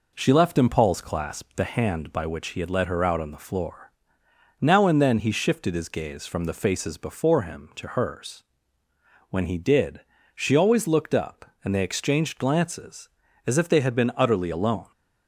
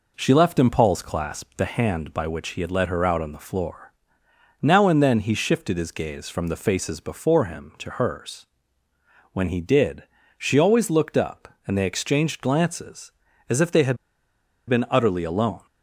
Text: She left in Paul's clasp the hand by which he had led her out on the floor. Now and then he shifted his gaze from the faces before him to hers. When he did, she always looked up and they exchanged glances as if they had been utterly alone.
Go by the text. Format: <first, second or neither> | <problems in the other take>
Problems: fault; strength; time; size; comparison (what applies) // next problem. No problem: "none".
first | pauses between "had" and "been"; noticeable; at 13.9 s; 0.71 s long